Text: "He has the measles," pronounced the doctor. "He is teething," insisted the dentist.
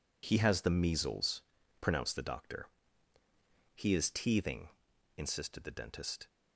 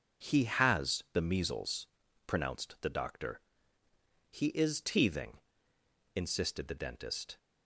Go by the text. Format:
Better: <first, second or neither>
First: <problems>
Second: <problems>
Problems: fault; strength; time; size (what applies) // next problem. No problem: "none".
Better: neither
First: none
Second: none